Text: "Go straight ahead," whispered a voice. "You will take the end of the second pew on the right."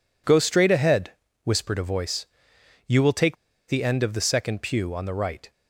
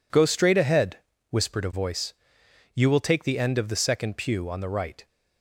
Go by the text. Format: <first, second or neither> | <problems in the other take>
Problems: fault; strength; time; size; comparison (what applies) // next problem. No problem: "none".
second | pauses between "take" and "the"; slight; at 3.3 s; 0.33 s long